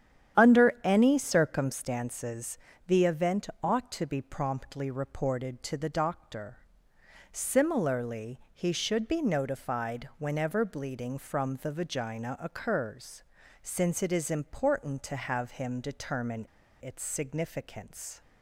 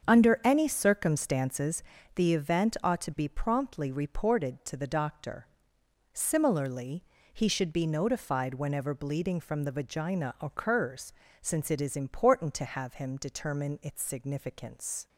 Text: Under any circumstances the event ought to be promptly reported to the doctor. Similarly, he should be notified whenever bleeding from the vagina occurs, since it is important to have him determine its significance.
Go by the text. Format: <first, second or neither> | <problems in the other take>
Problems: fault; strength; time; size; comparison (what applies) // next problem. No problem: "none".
second | starts louder than the rest; strong; until 1.4 s; 9.5 dB; strong in the second // pauses between "circumstances" and "the"; slight; at 2.5 s; 0.30 s long; slight in the second // pauses between "event" and "ought"; slight; at 3.4 s; 0.16 s long // pauses between "determine" and "its"; slight; at 16.4 s; 0.35 s long